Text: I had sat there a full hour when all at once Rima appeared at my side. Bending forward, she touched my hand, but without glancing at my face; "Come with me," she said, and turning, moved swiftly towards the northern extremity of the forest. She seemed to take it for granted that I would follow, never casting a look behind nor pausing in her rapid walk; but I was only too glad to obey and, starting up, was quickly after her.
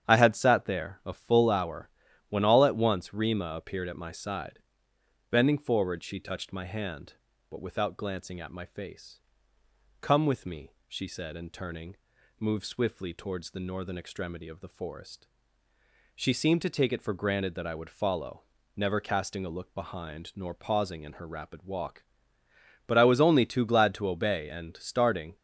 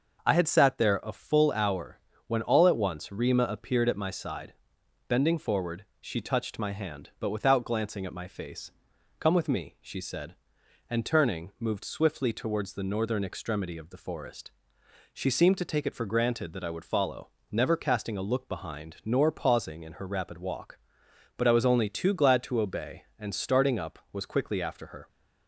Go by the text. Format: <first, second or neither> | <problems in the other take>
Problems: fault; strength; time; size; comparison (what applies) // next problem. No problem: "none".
second | starts louder than the rest; strong; until 1.1 s; 9 dB; noticeable in the second // pauses between "hour" and "when"; at 1.8 s; 0.40 s long; slight in the second // stops before "up was quickly after her"; at 25.3 s